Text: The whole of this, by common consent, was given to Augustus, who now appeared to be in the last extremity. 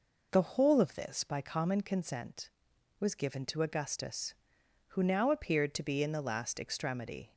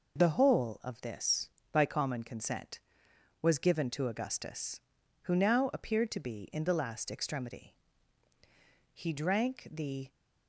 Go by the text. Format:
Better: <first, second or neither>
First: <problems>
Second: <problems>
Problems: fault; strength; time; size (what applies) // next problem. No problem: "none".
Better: first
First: none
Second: goes on to say "He drank the"; noticeable; from 8.9 s on; 1.1 s long